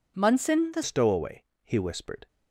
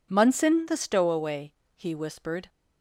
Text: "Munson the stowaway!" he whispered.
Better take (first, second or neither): second